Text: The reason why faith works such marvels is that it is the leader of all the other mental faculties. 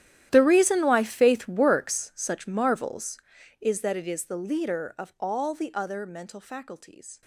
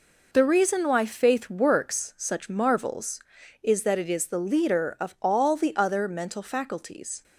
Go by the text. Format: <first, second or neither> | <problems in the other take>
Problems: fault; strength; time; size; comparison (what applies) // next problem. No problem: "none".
second | gets quieter; strong; throughout; 19.5 dB